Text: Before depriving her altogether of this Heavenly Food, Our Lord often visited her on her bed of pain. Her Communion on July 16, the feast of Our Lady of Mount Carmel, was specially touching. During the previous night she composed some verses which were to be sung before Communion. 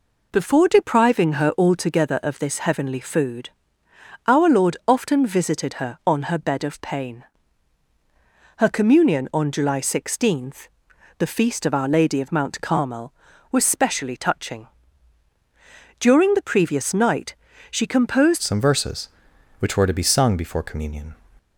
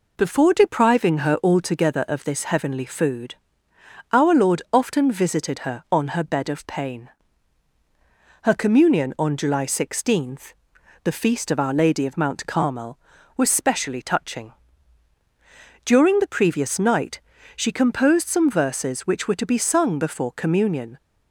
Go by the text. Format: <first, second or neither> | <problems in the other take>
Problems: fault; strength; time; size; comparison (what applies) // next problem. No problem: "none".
second | pauses between "night" and "she"; at 17.3 s; 0.38 s long; also in the second // changes voice at "some"; from 18.4 s on; 2.7 s long